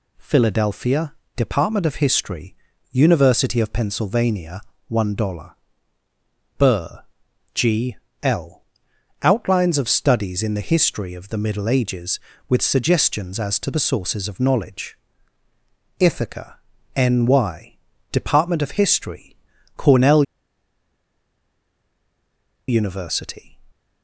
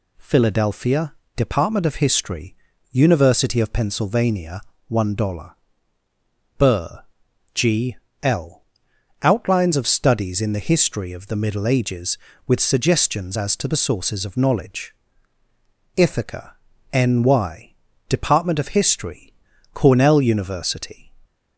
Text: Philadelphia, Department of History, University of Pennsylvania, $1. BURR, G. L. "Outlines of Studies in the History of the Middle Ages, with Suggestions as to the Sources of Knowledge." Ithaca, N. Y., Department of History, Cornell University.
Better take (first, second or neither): second